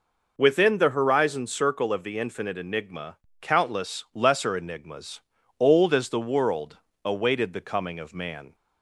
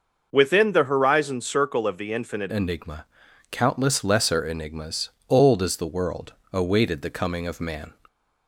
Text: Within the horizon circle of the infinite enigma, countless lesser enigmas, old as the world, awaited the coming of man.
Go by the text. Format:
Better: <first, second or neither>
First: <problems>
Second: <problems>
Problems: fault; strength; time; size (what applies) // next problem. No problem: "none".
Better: first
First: none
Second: changes voice at "enigma"; from 2.5 s on; 5.4 s long